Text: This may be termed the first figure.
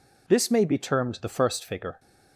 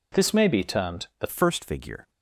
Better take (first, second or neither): first